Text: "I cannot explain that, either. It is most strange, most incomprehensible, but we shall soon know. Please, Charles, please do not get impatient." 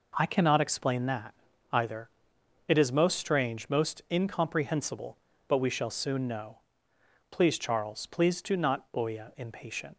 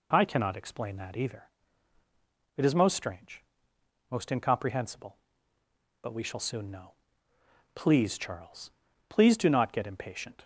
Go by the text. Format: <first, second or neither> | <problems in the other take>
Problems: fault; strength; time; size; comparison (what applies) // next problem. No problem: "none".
second | says "boya" for "get"; at 8.9 s